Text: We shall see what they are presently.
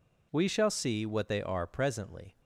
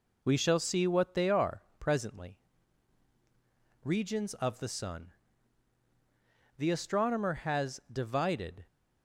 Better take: first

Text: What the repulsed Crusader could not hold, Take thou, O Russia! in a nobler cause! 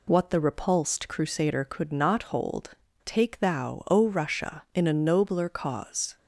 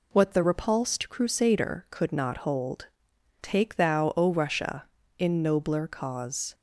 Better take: first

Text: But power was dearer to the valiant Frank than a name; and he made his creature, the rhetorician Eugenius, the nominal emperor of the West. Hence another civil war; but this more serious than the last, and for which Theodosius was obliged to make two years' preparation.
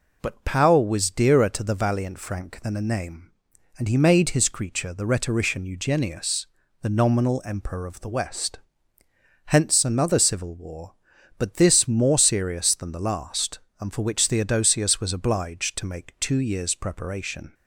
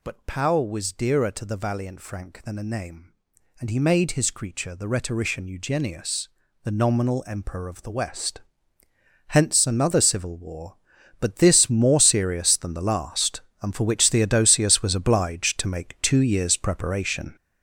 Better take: first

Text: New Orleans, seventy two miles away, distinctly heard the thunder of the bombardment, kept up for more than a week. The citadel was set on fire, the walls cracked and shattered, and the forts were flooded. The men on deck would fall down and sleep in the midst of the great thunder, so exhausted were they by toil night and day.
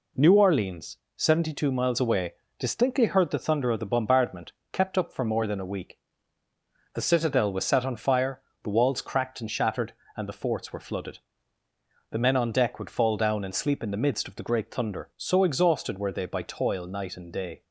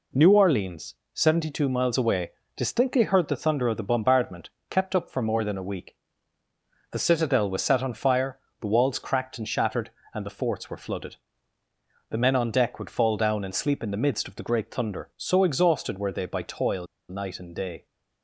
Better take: first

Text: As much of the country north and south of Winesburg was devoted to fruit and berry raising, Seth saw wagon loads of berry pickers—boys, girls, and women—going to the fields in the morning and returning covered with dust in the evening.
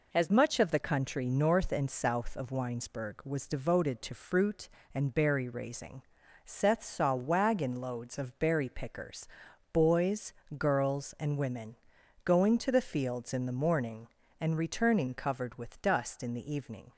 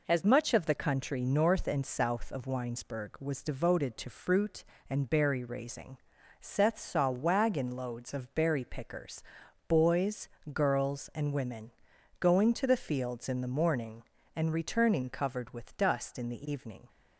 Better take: neither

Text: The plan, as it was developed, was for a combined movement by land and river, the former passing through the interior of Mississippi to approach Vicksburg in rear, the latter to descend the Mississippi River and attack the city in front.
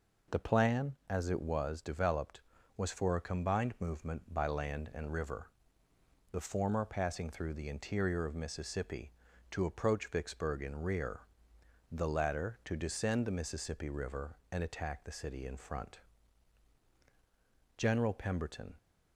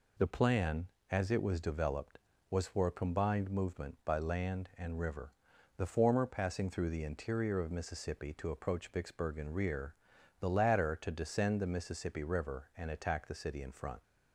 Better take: second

